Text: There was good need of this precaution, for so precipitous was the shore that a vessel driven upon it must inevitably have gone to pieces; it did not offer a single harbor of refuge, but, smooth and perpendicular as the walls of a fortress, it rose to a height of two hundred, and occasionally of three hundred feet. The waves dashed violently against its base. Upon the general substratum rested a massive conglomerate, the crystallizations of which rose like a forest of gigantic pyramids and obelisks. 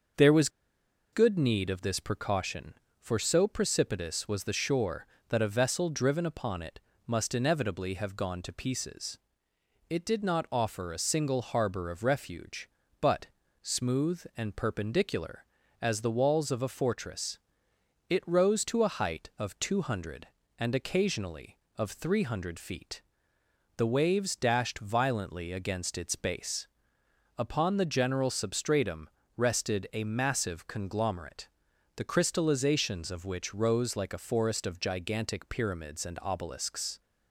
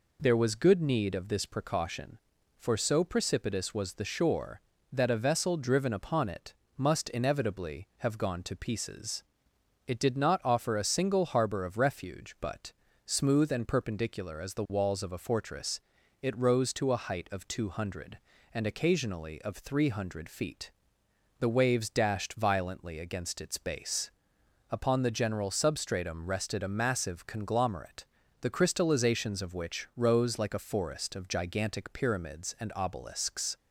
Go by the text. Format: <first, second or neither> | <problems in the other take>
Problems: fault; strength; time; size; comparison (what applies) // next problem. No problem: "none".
second | starts louder than the rest; until 1.8 s; 6.5 dB // pauses between "was" and "good"; noticeable; at 0.4 s; 0.64 s long // pauses between "it" and "must"; slight; at 6.7 s; 0.26 s long; slight in the second // pauses between "substratum" and "rested"; slight; at 29.0 s; 0.30 s long